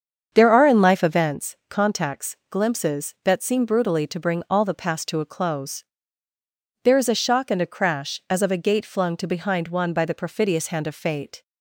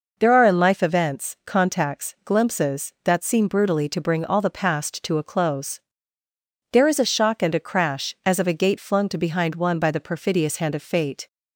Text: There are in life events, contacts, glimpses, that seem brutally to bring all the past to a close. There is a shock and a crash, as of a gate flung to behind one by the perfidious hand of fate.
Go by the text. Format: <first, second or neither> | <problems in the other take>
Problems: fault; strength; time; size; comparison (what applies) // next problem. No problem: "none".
second | starts louder than the rest; strong; until 1.4 s; 7.5 dB